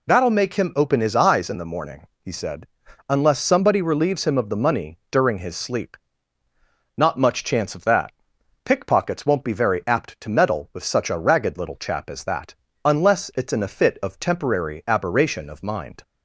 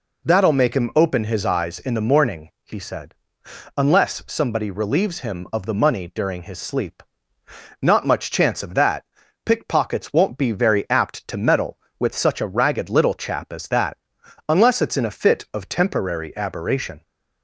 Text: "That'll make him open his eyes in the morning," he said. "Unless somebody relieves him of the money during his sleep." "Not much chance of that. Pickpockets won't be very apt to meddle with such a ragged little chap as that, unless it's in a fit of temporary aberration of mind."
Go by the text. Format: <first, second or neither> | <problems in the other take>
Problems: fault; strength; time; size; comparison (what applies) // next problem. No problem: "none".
first | stops before "of mind"; at 17.0 s